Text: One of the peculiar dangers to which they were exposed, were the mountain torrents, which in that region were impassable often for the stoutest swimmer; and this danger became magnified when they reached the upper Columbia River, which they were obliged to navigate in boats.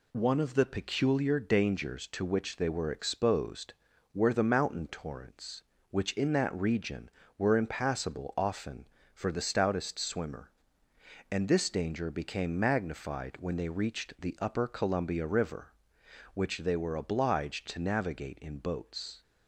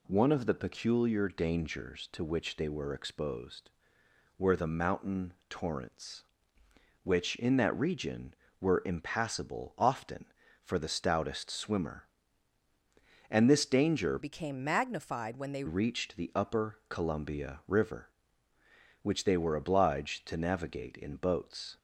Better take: first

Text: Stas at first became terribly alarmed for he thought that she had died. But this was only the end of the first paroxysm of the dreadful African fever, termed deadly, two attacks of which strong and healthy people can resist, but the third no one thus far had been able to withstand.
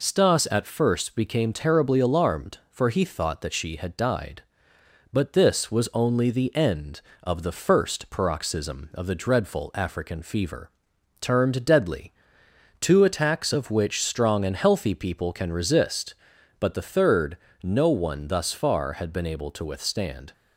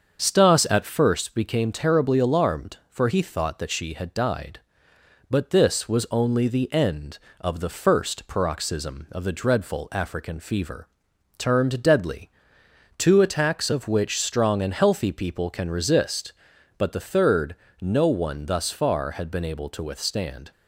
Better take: first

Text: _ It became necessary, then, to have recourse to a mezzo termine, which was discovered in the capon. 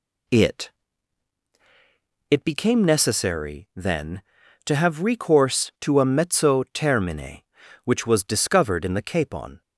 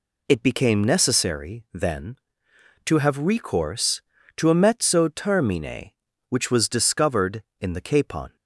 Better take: second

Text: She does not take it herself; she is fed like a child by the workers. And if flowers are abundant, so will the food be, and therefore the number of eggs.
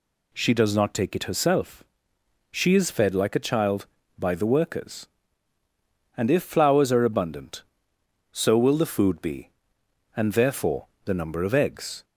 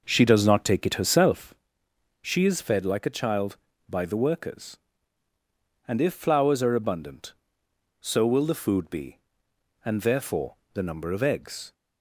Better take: first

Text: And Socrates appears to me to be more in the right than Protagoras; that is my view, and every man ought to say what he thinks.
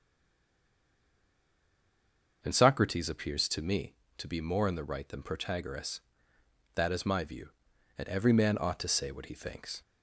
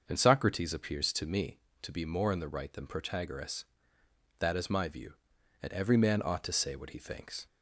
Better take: second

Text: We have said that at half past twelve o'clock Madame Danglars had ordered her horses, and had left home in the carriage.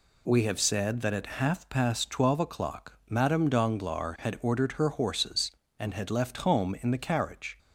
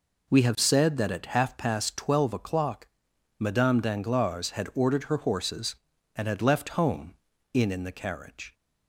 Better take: first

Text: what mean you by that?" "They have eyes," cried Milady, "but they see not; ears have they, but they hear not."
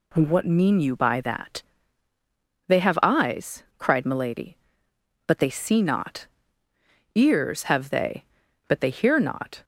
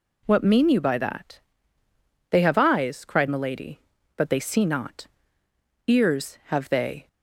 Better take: first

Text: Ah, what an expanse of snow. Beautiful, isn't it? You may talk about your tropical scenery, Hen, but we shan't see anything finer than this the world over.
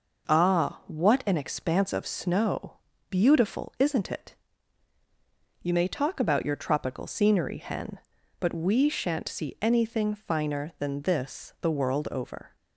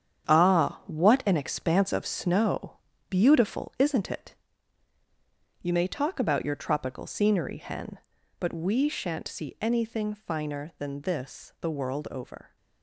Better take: first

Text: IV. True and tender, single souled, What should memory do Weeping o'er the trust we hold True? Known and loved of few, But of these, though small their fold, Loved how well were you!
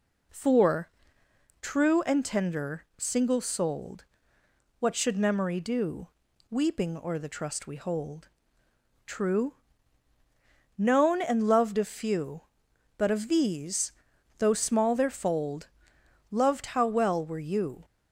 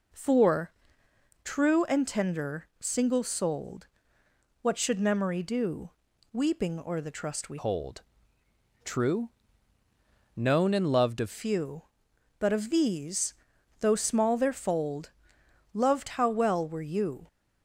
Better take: first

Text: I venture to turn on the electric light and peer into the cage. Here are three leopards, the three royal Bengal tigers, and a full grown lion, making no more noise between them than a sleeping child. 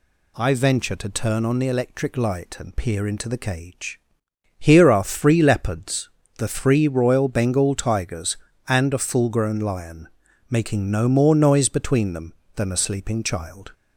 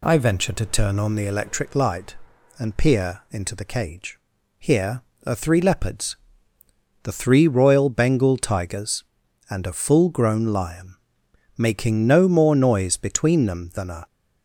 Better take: first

